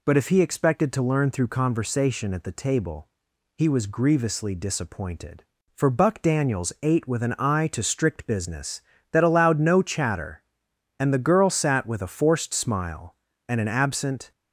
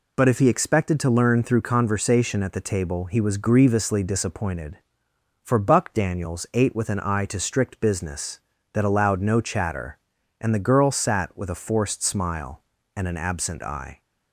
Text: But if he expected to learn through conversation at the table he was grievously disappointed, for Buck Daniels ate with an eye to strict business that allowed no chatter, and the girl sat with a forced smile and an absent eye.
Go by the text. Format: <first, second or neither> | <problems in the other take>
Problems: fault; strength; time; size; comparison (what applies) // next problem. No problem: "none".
second | pauses between "table" and "he"; noticeable; at 3.0 s; 0.50 s long // stops before "eye"; at 14.3 s